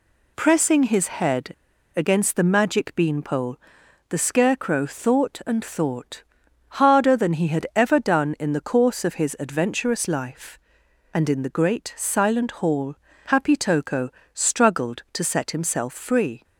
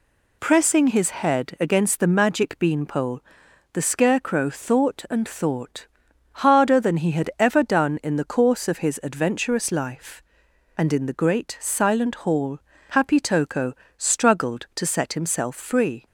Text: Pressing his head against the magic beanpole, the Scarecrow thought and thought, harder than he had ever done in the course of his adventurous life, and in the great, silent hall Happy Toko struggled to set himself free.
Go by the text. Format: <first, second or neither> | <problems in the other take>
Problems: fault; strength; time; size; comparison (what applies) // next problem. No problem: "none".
second | pauses between "head" and "against"; at 1.5 s; 0.42 s long // pauses between "hall" and "Happy"; slight; at 12.9 s; 0.32 s long; slight in the second // pauses between "Toko" and "struggled"; slight; at 14.0 s; 0.24 s long; slight in the second